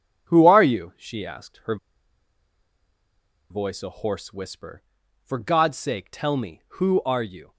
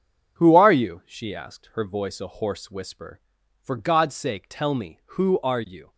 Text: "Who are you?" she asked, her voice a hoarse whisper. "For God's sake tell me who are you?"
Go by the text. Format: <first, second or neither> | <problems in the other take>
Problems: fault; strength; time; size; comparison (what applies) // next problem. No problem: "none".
second | pauses between "her" and "voice"; strong; at 1.7 s; 1.7 s long